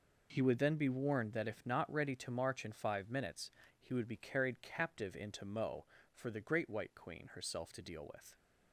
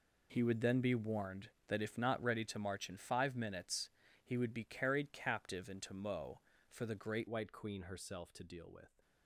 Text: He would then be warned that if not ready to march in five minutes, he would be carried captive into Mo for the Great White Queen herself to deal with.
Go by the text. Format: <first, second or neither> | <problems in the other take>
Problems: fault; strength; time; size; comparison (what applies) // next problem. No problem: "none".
first | changes voice at "White"; from 7.2 s on; 1.8 s long